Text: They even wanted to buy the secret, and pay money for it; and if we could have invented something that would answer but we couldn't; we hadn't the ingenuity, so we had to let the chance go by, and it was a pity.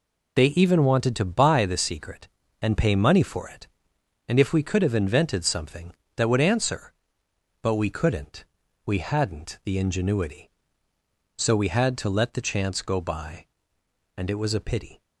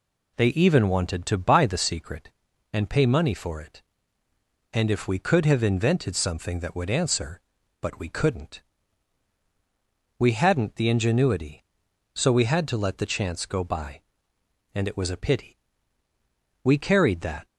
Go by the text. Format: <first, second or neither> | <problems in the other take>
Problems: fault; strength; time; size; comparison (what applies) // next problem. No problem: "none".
first | goes on to say "We carried that"; noticeable; from 16.6 s on; 0.82 s long